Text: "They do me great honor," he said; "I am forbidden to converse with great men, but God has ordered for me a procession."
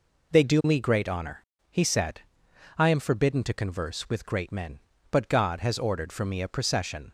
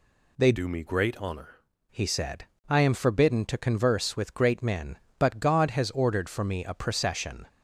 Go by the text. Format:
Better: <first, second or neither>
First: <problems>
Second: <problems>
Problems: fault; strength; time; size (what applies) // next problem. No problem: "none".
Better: first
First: none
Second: changes voice from "do" to "honor"; from 0.5 to 1.6 s; 1.1 s long